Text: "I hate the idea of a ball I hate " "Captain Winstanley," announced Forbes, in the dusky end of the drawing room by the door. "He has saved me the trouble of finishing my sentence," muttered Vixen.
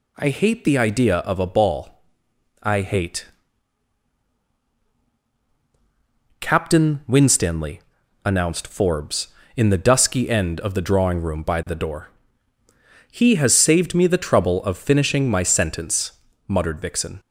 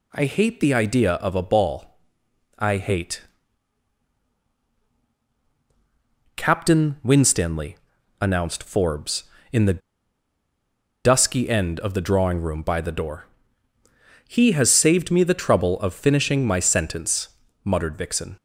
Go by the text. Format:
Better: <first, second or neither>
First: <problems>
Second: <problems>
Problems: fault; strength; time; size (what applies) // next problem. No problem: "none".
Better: first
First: pauses between "ball" and "I"; noticeable; at 2.0 s; 0.62 s long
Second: pauses between "ball" and "I"; noticeable; at 1.9 s; 0.62 s long // pauses between "the" and "dusky"; at 9.8 s; 1.2 s long